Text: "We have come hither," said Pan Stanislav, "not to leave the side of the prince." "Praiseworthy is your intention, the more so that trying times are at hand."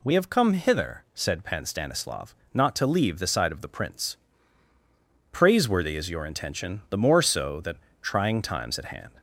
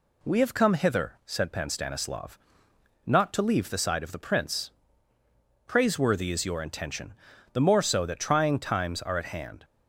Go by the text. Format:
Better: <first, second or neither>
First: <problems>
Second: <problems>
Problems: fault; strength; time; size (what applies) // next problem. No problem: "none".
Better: second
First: pauses between "that" and "trying"; slight; at 7.7 s; 0.24 s long // skips "are"; at 8.7 s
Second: none